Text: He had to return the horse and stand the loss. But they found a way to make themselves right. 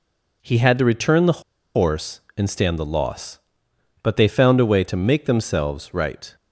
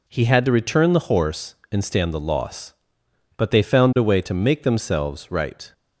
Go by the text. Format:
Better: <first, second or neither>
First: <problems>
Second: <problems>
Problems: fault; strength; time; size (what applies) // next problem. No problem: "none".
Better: second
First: pauses between "the" and "horse"; slight; at 1.4 s; 0.34 s long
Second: none